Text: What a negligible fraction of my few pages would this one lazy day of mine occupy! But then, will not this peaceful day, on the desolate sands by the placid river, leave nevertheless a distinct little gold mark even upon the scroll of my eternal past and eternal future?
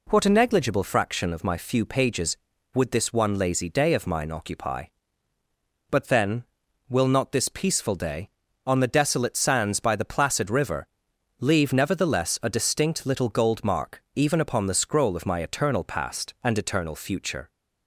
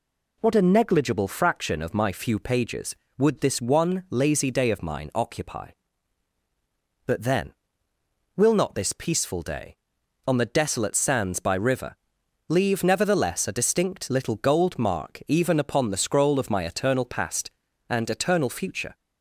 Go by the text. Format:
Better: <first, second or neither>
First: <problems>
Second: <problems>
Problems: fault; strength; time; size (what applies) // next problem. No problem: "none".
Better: first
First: none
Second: skips "the placid"; at 11.5 s